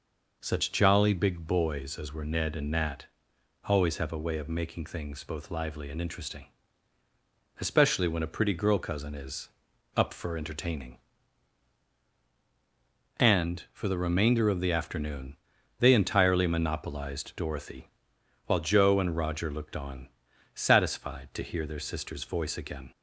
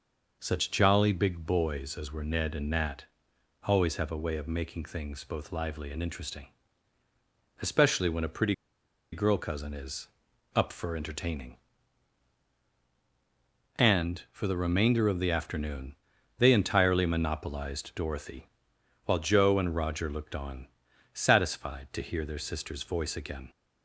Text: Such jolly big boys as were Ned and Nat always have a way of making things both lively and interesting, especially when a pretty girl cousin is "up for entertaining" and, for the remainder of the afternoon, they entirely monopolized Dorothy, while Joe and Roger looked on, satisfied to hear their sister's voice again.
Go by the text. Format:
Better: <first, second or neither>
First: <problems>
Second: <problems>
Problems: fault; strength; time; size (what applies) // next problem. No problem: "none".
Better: first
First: pauses between "Nat" and "always"; noticeable; at 3.0 s; 0.62 s long // pauses between "is" and "up"; noticeable; at 9.4 s; 0.48 s long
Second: pauses between "Nat" and "always"; noticeable; at 3.0 s; 0.62 s long // pauses between "pretty" and "girl"; noticeable; at 8.5 s; 0.58 s long // pauses between "is" and "up"; noticeable; at 10.0 s; 0.48 s long